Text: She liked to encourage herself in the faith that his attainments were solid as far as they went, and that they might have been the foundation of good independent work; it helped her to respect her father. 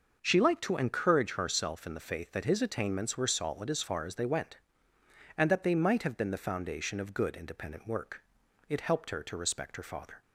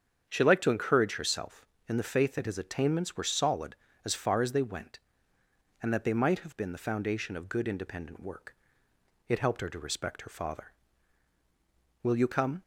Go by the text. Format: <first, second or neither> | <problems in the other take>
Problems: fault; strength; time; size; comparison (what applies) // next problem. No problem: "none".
first | starts louder than the rest; strong; until 1.3 s; 8 dB // goes on to say "Will you come"; from 12.0 s on; 0.60 s long